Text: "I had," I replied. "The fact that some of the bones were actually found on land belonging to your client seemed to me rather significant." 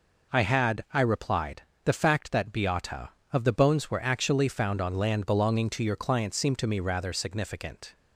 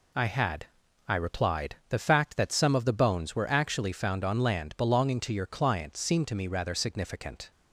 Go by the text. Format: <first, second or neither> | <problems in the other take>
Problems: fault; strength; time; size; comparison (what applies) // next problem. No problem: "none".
second | says "beata" for "some"; at 2.5 s